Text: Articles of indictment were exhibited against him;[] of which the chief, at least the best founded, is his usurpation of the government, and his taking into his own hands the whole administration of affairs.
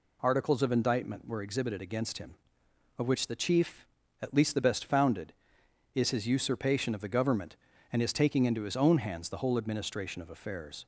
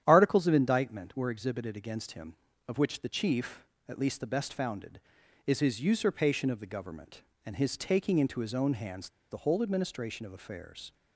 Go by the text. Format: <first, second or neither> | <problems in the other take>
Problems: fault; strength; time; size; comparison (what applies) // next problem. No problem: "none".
first | starts louder than the rest; strong; until 1.0 s; 10 dB // pauses between "hands" and "the"; slight; at 9.0 s; 0.23 s long